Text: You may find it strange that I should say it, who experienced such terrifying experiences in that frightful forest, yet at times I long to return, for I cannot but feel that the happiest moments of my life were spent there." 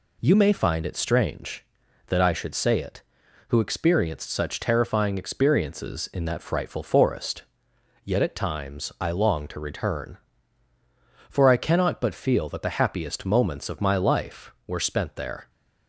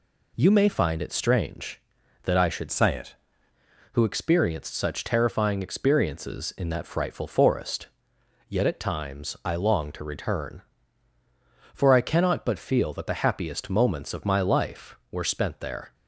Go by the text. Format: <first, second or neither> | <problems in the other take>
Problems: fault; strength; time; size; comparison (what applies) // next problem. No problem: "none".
first | changes voice from "say" to "it"; from 2.7 to 3.1 s; 0.4 s long